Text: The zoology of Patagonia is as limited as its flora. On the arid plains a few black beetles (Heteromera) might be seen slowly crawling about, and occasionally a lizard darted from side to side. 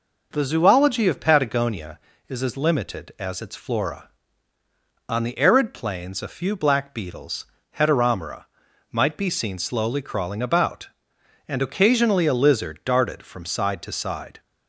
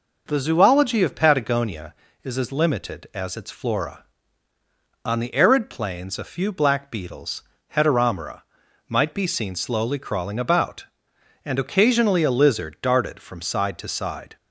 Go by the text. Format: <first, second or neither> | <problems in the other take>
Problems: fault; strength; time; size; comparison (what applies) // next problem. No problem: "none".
neither | none